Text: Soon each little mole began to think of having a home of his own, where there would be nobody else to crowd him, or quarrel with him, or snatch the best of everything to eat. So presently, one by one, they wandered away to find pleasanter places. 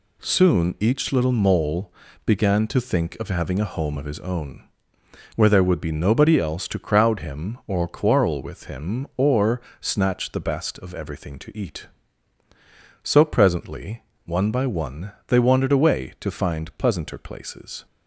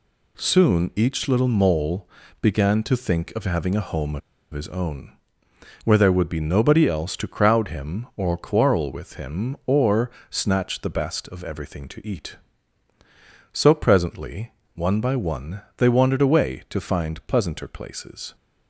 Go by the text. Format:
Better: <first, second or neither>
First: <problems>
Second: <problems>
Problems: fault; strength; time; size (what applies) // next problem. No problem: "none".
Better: first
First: pauses between "mole" and "began"; slight; at 1.9 s; 0.36 s long // pauses between "or" and "snatch"; slight; at 9.6 s; 0.18 s long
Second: pauses between "mole" and "began"; slight; at 2.0 s; 0.36 s long // pauses between "of" and "his"; slight; at 4.2 s; 0.32 s long // pauses between "or" and "snatch"; slight; at 10.1 s; 0.18 s long